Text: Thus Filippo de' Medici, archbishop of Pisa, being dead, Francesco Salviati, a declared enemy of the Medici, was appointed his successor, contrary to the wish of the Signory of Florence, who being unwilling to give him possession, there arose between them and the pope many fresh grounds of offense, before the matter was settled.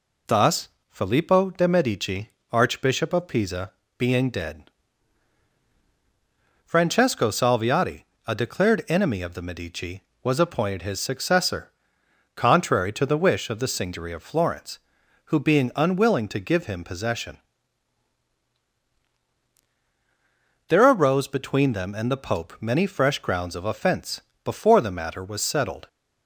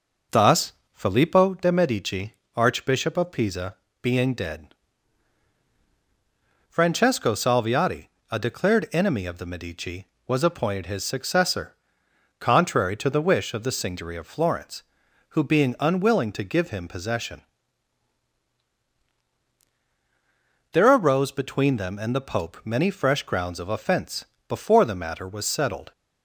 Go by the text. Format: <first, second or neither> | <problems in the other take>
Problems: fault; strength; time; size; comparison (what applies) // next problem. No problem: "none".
first | starts louder than the rest; noticeable; until 1.6 s; 5.5 dB // pauses between "Thus" and "Filippo"; slight; at 0.7 s; 0.20 s long; slight in the first